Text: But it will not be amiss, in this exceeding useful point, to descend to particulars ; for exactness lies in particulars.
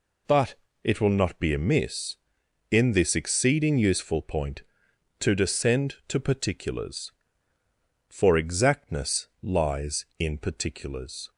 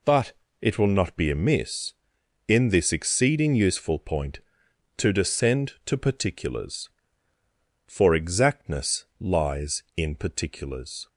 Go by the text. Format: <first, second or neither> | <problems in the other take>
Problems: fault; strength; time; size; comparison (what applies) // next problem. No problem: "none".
neither | pauses between "But" and "it"; slight; the same in both // pauses between "exactness" and "lies"; slight; the same in both